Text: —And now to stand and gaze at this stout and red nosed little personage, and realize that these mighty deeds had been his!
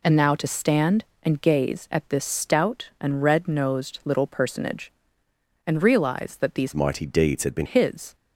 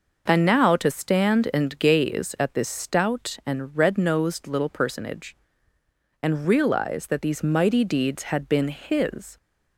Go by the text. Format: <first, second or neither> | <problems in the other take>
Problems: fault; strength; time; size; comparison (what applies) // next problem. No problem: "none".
second | changes voice from "mighty" to "been"; from 6.7 to 7.6 s; 0.9 s long